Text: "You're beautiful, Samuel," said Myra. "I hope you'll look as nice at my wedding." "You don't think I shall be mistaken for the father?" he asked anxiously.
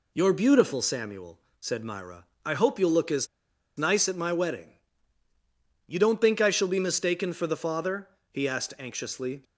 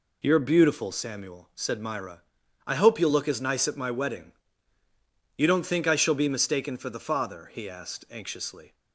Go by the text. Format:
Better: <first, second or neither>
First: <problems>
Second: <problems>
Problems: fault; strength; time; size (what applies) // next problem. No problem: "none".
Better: second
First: pauses between "as" and "nice"; noticeable; at 3.2 s; 0.50 s long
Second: none